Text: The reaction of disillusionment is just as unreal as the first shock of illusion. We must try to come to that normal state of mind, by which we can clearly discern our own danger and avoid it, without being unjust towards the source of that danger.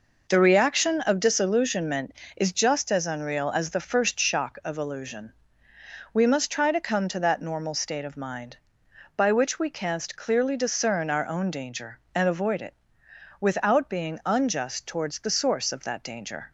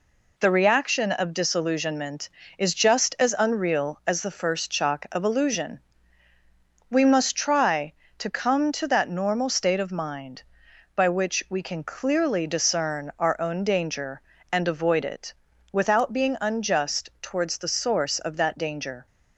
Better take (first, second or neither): second